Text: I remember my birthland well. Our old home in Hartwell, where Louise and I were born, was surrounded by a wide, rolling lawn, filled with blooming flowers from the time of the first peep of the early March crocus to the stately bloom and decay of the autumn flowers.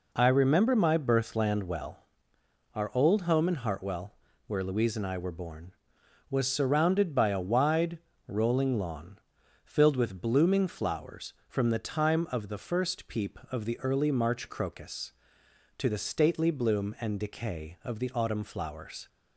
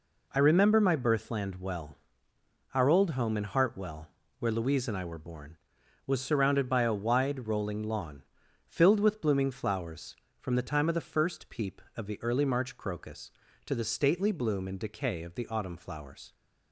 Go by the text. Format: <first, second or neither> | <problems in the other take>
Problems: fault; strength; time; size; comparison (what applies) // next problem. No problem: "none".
neither | none